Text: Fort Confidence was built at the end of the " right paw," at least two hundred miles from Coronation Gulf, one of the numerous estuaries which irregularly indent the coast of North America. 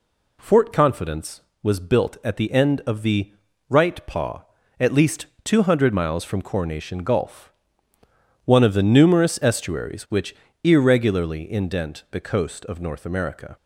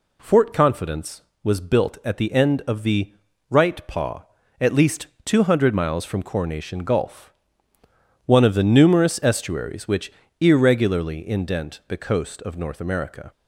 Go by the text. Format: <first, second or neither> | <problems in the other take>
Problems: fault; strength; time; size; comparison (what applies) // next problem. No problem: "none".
neither | pauses between "least" and "two"; slight; the same in both // pauses between "which" and "irregularly"; slight; the same in both